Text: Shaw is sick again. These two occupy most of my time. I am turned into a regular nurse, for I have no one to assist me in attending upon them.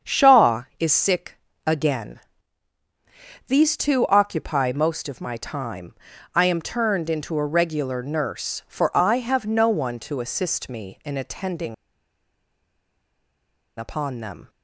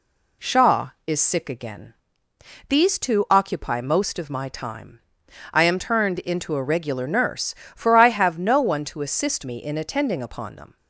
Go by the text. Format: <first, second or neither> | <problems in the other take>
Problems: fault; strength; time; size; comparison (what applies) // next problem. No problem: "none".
second | starts louder than the rest; strong; until 1.1 s; 7.5 dB // pauses between "sick" and "again"; slight; at 1.3 s; 0.30 s long // pauses between "attending" and "upon"; strong; at 11.7 s; 2.0 s long